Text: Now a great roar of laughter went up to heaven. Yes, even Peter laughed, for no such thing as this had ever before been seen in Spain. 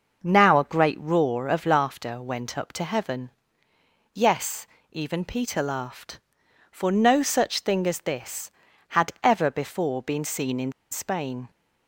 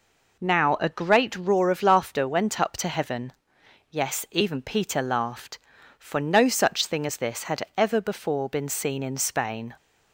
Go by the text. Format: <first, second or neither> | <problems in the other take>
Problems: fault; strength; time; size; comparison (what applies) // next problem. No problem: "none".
second | pauses between "in" and "Spain"; slight; at 10.7 s; 0.19 s long